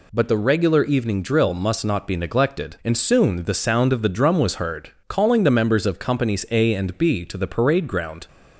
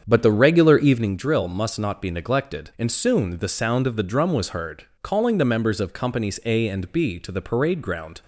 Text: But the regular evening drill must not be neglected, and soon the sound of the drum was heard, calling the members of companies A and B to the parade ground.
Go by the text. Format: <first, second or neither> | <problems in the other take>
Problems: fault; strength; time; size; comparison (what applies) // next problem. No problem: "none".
first | starts louder than the rest; strong; until 1.2 s; 7.5 dB